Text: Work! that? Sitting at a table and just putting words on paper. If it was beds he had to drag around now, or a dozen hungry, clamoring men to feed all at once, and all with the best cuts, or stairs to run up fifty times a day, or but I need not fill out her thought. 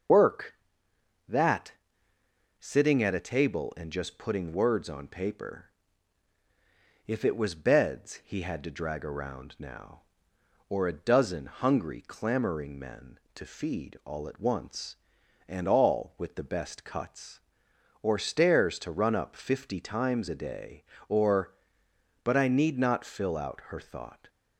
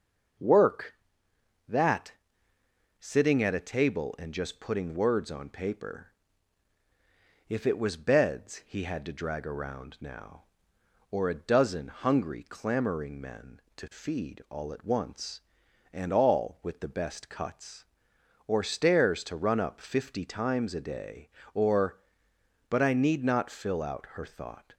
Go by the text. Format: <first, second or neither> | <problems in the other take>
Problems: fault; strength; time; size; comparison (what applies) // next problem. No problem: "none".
second | loses the start of "Work"; at 0.0 s; 110 ms // starts louder than the rest; noticeable; until 2.7 s; 6 dB